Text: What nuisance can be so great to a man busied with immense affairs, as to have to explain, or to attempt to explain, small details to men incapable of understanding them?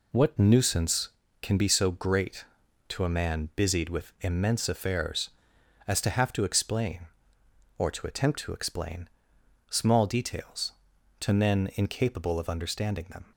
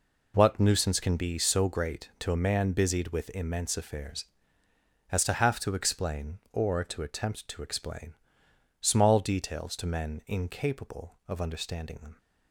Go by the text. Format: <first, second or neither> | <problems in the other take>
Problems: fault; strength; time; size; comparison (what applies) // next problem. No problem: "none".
neither | none